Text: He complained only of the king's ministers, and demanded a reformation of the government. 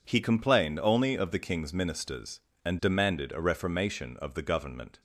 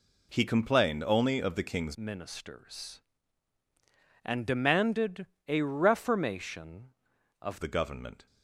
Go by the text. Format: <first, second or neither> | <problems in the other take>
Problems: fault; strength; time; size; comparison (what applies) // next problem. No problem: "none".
first | changes voice from "ministers" to "of"; from 1.9 to 7.6 s; 5.7 s long // pauses between "demanded" and "a"; slight; at 5.2 s; 0.20 s long